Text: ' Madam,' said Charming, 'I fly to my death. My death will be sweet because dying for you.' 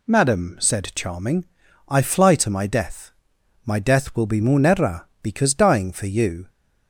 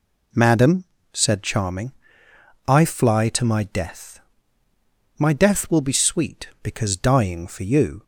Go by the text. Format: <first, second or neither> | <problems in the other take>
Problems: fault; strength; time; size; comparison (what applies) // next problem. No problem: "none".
second | says "munera" for "sweet"; at 4.4 s